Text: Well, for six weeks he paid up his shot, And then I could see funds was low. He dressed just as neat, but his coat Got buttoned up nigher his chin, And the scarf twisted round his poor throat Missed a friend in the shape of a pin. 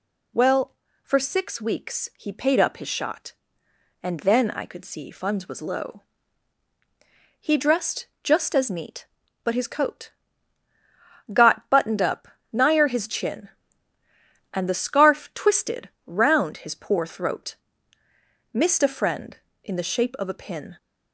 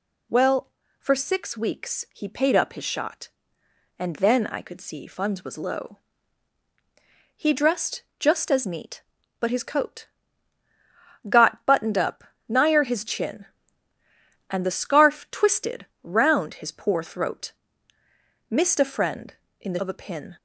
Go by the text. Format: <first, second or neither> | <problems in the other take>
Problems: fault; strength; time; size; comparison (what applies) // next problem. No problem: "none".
first | pauses between "dressed" and "just"; slight; at 8.0 s; 0.16 s long; slight in the first // pauses between "coat" and "Got"; at 10.0 s; 1.2 s long; also in the first // pauses between "up" and "nigher"; slight; at 12.2 s; 0.26 s long; slight in the first // pauses between "twisted" and "round"; slight; at 15.8 s; 0.18 s long; slight in the first // pauses between "throat" and "Missed"; noticeable; at 17.5 s; 0.96 s long; noticeable in the first // skips "shape"; at 19.7 s